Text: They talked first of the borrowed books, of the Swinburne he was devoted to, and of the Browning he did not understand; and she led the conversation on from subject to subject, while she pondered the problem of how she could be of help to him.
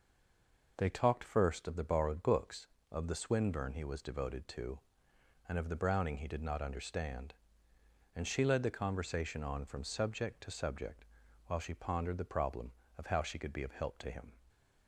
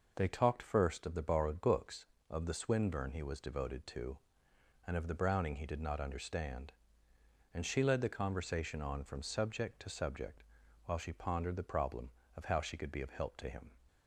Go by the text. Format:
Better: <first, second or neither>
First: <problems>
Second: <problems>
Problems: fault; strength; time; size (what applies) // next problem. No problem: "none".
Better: second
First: stays silent before the first word; slight; until 0.7 s; 0.7 s long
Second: none